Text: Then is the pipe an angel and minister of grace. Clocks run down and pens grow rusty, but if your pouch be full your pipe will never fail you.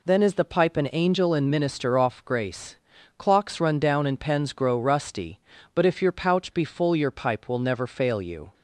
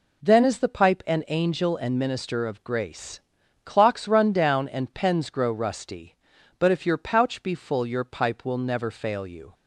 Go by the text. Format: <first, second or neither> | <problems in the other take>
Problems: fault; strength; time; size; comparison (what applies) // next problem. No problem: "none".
second | says "off" for "of"; at 1.9 s